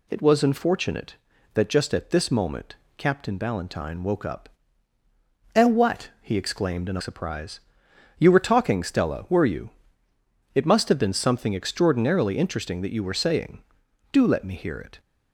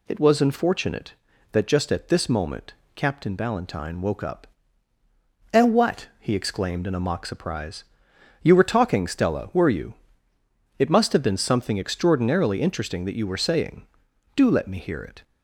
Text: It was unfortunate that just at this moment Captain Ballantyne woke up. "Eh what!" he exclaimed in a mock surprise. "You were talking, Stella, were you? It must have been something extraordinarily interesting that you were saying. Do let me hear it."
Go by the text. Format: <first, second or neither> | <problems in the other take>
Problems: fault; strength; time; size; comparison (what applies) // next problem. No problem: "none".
second | pauses between "moment" and "Captain"; slight; at 2.7 s; 0.20 s long; slight in the second // skips "mock"; at 7.0 s